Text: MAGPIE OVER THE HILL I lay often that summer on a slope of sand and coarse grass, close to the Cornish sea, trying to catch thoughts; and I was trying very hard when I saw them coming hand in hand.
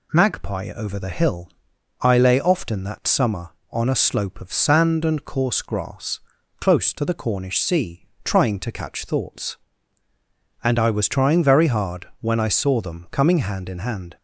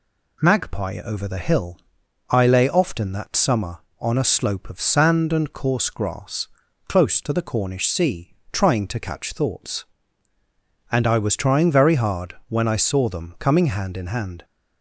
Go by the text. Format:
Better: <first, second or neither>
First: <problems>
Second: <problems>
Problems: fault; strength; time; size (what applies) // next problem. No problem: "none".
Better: neither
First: pauses between "HILL" and "I"; noticeable; at 1.5 s; 0.50 s long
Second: pauses between "HILL" and "I"; noticeable; at 1.8 s; 0.50 s long